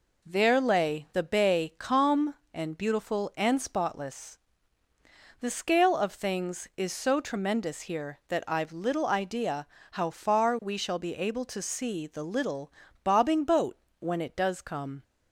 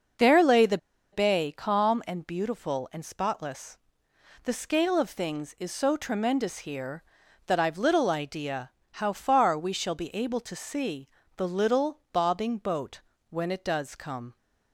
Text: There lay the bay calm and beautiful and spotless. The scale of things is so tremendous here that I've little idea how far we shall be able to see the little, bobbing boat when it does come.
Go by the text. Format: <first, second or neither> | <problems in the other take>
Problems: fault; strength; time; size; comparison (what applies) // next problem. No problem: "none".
first | pauses between "the" and "bay"; slight; at 0.7 s; 0.35 s long // pauses between "idea" and "how"; slight; at 8.6 s; 0.24 s long; slight in the first // pauses between "see" and "the"; slight; at 11.0 s; 0.28 s long // pauses between "boat" and "when"; slight; at 13.0 s; 0.28 s long; slight in the first